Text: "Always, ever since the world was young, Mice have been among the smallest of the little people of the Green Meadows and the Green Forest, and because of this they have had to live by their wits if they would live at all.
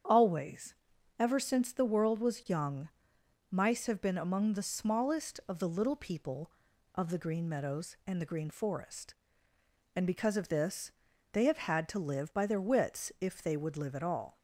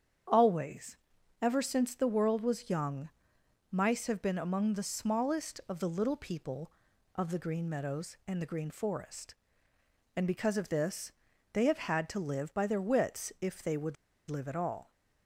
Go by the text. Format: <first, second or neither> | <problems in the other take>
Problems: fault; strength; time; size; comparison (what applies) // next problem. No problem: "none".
first | starts louder than the rest; strong; until 1.7 s; 8 dB; strong in the first // pauses between "this" and "they"; at 11.1 s; 0.42 s long; also in the first // pauses between "would" and "live"; slight; at 13.9 s; 0.33 s long